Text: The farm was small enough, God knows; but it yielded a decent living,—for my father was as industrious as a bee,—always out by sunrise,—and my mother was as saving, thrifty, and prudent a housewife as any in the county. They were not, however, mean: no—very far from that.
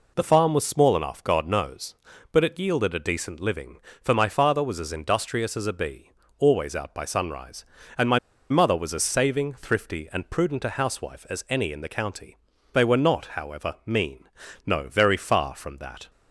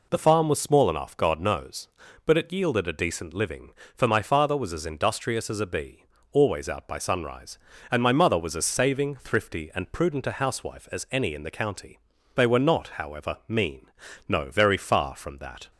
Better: second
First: pauses between "my" and "mother"; slight; at 8.1 s; 0.31 s long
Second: none

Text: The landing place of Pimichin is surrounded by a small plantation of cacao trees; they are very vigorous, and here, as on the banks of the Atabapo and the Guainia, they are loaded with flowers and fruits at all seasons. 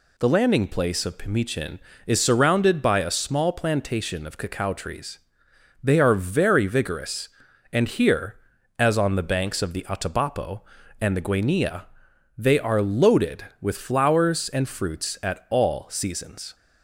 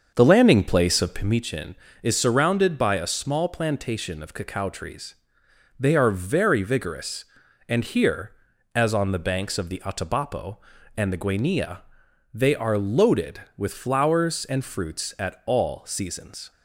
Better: first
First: none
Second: starts louder than the rest; until 1.4 s; 7 dB

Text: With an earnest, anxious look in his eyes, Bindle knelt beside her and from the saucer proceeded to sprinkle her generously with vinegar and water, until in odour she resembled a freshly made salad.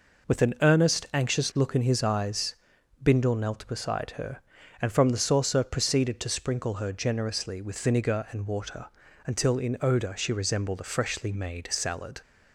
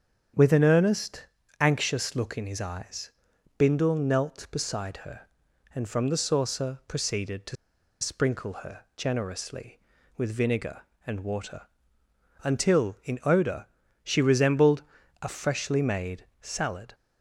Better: first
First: none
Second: starts louder than the rest; strong; until 1.7 s; 8 dB // pauses between "to" and "sprinkle"; noticeable; at 7.5 s; 0.46 s long // pauses between "odour" and "she"; at 13.6 s; 0.38 s long // pauses between "resembled" and "a"; at 14.8 s; 0.38 s long // pauses between "made" and "salad"; slight; at 16.2 s; 0.16 s long

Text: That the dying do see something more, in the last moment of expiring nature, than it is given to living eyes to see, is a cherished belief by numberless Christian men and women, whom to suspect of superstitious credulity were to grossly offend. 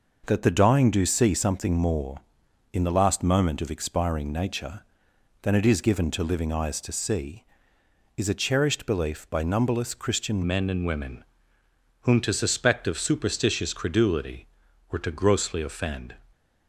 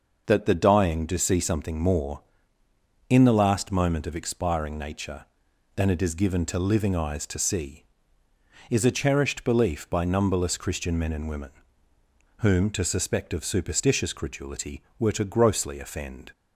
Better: second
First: changes voice at "men"; from 10.4 s on; 5.7 s long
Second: none

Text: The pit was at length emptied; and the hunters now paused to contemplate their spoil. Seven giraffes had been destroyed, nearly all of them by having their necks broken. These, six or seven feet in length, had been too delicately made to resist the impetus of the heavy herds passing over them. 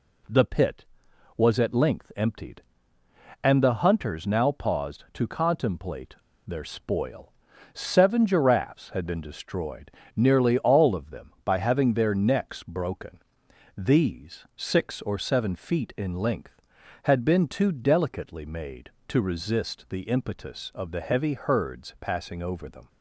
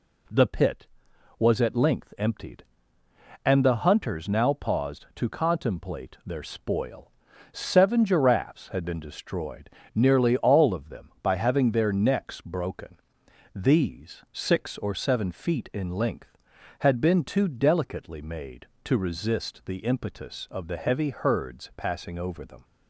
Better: second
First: pauses between "contemplate" and "their"; slight; at 6.1 s; 0.33 s long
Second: none

